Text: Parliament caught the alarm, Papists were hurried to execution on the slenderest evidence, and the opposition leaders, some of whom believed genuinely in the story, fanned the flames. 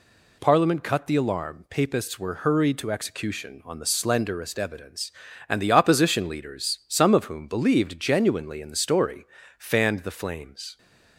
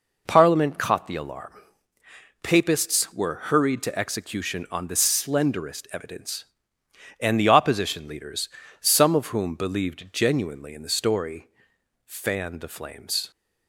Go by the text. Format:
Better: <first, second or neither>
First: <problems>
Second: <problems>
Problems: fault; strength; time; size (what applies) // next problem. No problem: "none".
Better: second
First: says "cut" for "caught"; at 0.8 s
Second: none